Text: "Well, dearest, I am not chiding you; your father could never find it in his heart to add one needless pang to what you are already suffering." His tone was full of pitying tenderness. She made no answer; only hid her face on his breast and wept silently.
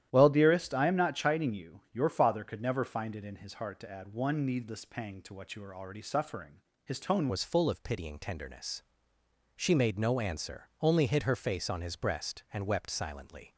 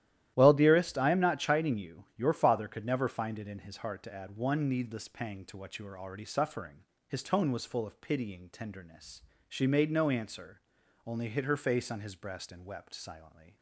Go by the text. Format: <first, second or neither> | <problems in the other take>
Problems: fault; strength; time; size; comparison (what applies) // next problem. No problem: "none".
second | starts louder than the rest; strong; until 1.1 s; 11.5 dB; strong in the second // changes voice at "was"; from 7.3 s on; 6.2 s long